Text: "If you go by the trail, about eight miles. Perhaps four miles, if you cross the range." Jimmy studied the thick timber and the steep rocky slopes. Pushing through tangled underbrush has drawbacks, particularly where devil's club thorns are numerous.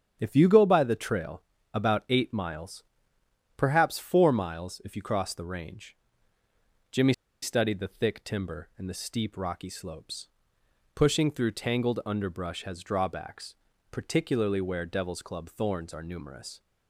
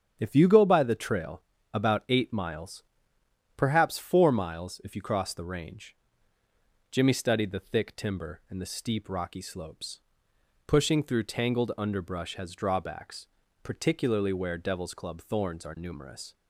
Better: second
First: starts louder than the rest; strong; until 1.2 s; 8 dB // pauses between "Jimmy" and "studied"; slight; at 7.1 s; 0.30 s long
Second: starts louder than the rest; strong; until 1.2 s; 8.5 dB

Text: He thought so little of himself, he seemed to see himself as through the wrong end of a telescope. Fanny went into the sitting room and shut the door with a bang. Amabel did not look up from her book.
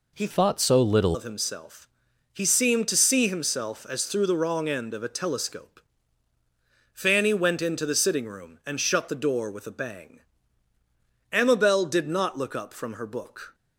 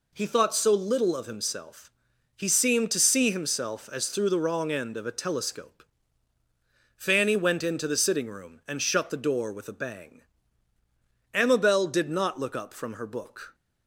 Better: second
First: changes voice from "thought" to "little"; from 0.3 to 1.1 s; 0.8 s long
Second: none

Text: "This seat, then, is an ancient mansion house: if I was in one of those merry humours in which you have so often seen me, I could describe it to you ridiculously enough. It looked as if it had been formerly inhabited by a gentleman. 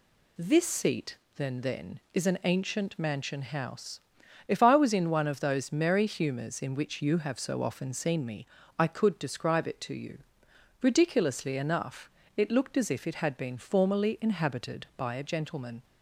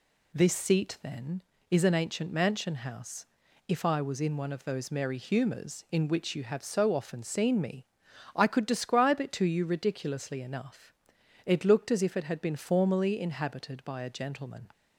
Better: second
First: says "then" twice; at 1.6 s // pauses between "you" and "ridiculously"; noticeable; at 10.1 s; 0.64 s long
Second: none

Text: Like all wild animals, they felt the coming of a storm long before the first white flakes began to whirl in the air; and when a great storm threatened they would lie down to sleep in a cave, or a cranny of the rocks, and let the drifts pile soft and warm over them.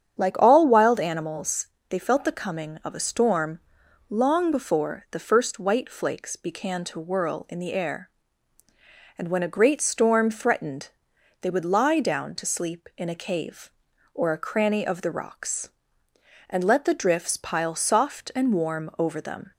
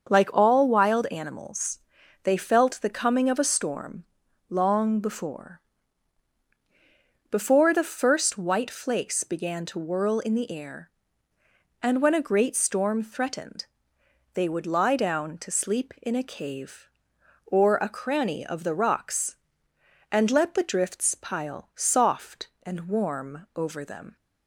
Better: first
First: starts louder than the rest; strong; until 1.2 s; 8.5 dB // pauses between "storm" and "long"; noticeable; at 3.5 s; 0.50 s long // pauses between "threatened" and "they"; noticeable; at 10.8 s; 0.52 s long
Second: starts louder than the rest; until 1.1 s; 7 dB // pauses between "storm" and "long"; at 4.0 s; 0.44 s long // says "before" twice; at 7.2 s // pauses between "threatened" and "they"; noticeable; at 13.6 s; 0.68 s long

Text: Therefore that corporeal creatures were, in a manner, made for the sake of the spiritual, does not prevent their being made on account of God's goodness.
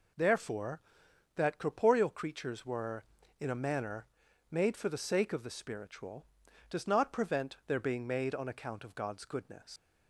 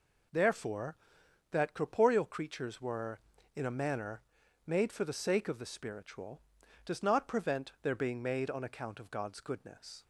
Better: second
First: leaves "goodness" unfinished; at 9.7 s; 115 ms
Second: none

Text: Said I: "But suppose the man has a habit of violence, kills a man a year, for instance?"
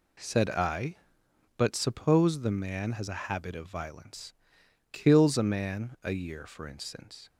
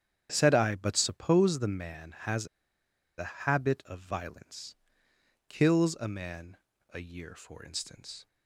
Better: first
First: none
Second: starts louder than the rest; strong; until 1.3 s; 8.5 dB // pauses between "has" and "a"; noticeable; at 2.4 s; 0.71 s long // pauses between "man" and "a"; slight; at 6.5 s; 0.34 s long

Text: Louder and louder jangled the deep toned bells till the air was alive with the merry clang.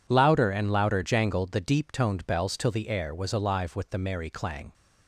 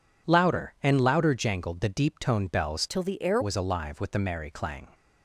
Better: first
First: none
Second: changes voice from "till" to "air"; from 2.8 to 3.3 s; 0.5 s long

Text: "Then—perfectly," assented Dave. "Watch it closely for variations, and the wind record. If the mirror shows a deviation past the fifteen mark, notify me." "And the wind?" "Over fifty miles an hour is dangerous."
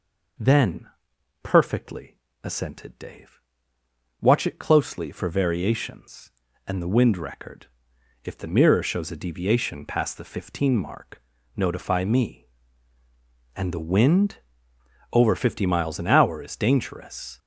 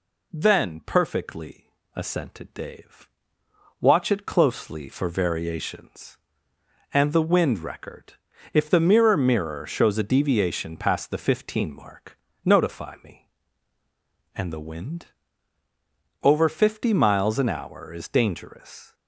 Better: first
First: none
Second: says "mirror" twice; at 9.1 s

